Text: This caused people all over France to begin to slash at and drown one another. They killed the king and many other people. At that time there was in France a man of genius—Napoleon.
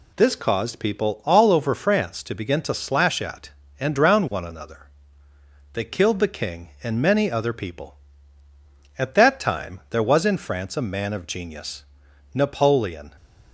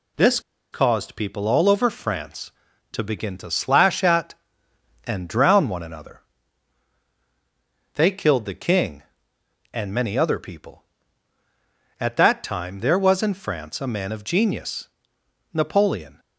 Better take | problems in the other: first | pauses between "This" and "caused"; slight; at 0.3 s; 0.32 s long

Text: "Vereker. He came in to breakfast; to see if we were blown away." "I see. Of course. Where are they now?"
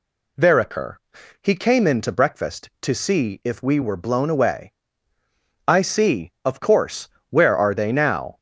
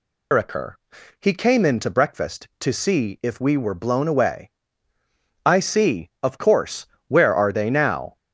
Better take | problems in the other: first | loses the start of "Vereker"; at 0.3 s; 150 ms

